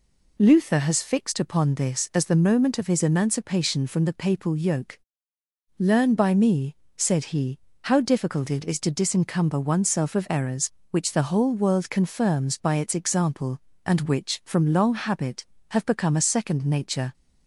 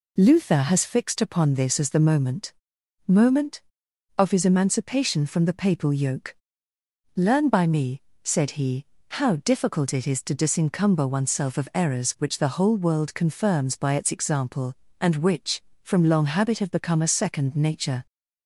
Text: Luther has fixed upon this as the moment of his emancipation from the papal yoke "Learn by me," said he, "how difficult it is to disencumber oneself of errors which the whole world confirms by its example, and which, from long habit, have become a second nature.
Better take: first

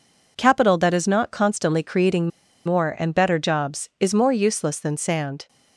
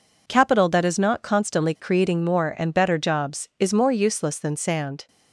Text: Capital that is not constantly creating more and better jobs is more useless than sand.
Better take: second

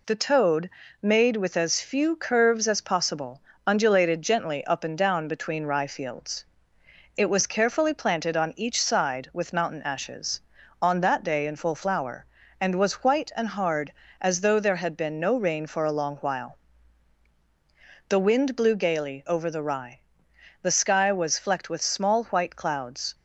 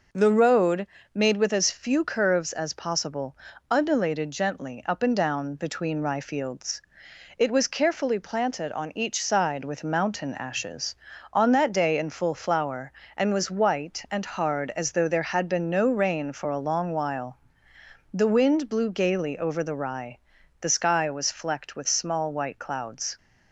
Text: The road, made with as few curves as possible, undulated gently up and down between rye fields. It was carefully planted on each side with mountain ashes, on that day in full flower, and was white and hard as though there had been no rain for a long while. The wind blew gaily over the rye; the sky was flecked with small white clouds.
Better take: second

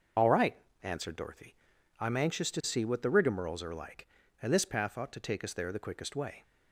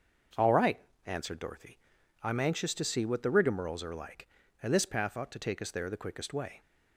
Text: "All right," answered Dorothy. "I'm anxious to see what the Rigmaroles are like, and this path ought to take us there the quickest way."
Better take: second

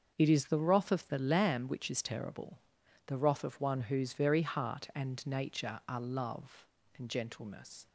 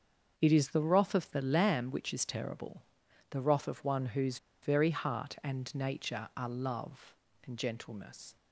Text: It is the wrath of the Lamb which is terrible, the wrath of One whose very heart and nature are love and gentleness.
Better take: first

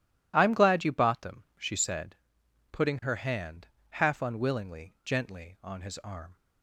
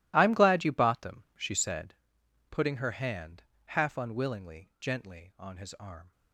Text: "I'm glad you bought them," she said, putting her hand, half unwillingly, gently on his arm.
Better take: first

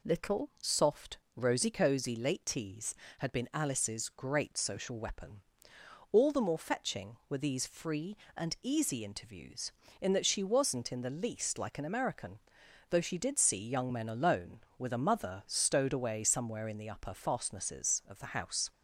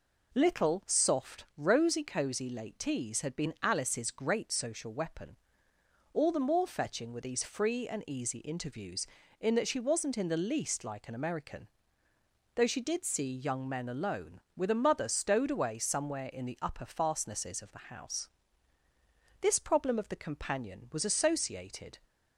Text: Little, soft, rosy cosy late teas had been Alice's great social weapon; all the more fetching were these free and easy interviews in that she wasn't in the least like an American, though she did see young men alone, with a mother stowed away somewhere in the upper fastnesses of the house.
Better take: first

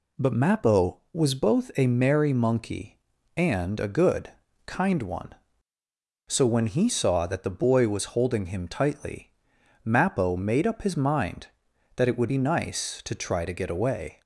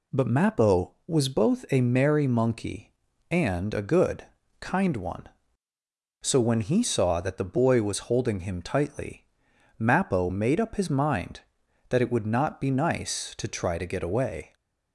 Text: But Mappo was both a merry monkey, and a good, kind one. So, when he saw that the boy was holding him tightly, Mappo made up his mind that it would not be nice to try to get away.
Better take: second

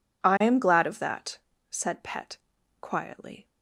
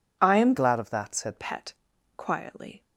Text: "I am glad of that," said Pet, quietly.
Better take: first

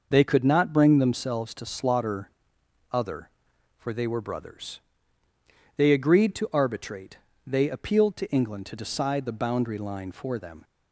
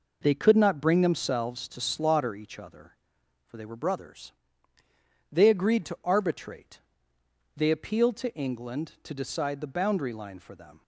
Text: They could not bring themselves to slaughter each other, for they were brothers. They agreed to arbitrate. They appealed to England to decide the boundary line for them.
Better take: second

